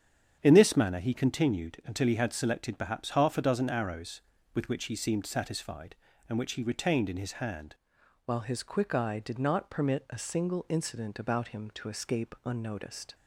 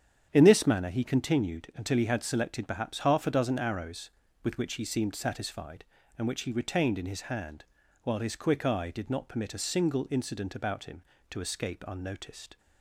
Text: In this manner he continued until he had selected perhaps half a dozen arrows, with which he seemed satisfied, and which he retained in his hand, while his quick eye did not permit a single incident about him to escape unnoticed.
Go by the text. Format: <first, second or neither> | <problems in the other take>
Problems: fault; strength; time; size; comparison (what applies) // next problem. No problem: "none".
second | starts louder than the rest; strong; until 1.4 s; 8 dB; strong in the second // changes voice at "while"; from 8.2 s on; 4.9 s long